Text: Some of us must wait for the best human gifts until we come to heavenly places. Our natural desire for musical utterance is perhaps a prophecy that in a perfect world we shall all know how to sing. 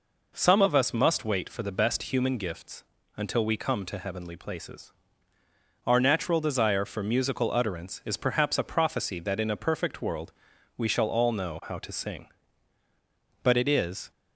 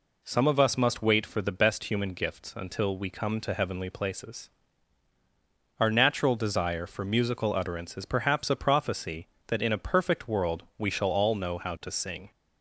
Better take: second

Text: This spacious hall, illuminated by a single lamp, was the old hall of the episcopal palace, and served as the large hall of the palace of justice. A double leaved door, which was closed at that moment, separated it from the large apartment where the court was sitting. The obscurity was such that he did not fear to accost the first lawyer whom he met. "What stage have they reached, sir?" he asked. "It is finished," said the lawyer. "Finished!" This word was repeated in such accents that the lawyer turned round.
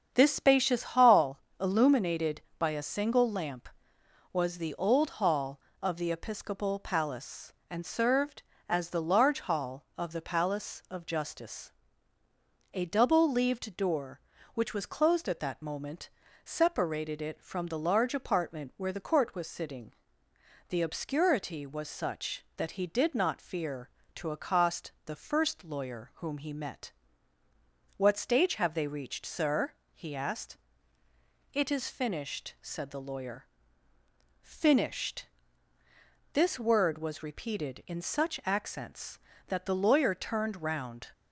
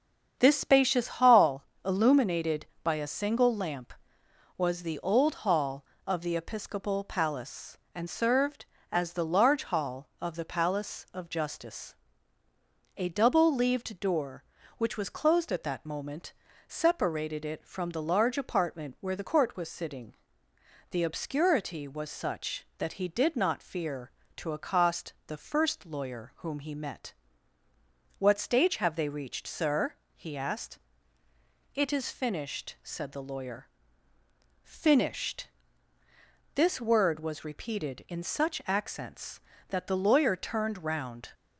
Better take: neither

